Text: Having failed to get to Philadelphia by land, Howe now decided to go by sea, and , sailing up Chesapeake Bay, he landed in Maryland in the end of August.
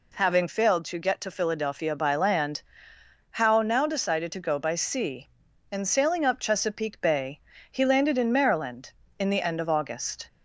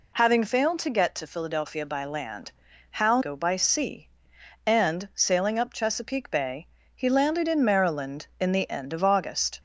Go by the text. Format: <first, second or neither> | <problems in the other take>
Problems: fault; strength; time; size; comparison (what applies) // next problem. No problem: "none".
first | skips "now decided to"; at 3.2 s